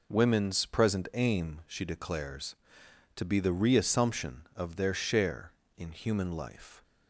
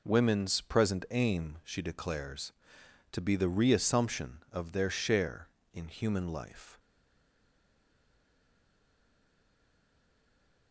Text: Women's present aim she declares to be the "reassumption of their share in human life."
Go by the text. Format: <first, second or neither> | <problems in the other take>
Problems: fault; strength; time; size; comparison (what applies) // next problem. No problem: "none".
first | stays silent after the last word; strong; from 6.7 s on; 4.0 s long